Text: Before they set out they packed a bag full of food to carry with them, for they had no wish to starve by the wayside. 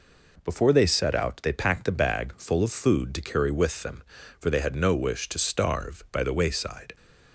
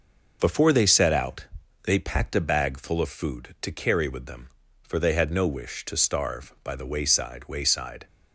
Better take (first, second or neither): first